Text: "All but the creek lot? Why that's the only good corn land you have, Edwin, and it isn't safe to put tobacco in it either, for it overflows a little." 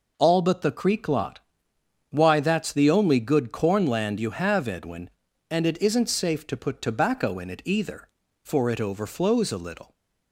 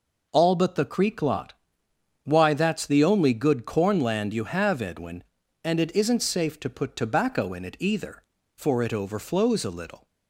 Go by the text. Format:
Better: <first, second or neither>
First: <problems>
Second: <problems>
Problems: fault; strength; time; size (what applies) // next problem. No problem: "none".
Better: neither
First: none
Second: none